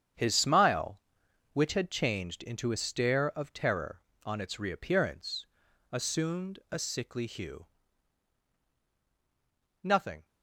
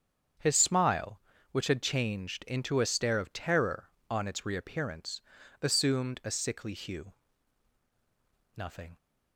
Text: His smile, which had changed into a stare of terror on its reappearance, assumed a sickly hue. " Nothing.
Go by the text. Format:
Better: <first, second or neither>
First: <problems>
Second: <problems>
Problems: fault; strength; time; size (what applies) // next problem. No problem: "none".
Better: second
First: gets quieter; strong; throughout; 35.5 dB // starts louder than the rest; strong; until 1.6 s; 9 dB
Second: starts louder than the rest; strong; until 1.7 s; 8.5 dB